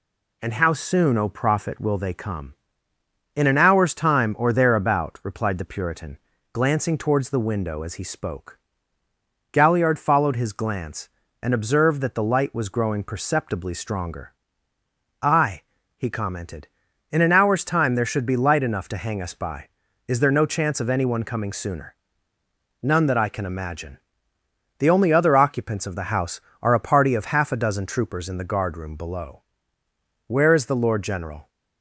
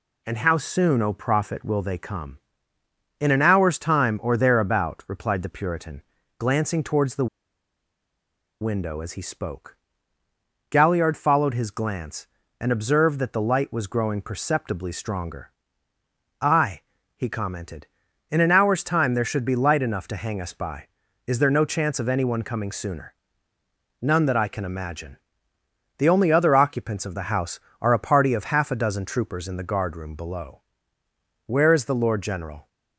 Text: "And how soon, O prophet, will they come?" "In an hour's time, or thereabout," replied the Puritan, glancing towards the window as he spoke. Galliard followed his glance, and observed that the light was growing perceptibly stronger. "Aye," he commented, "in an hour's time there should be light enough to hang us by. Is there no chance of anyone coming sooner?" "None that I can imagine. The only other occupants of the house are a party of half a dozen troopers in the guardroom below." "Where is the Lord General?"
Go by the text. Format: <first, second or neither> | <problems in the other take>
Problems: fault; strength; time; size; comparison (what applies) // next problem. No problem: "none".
first | pauses between "the" and "window"; strong; at 7.2 s; 1.3 s long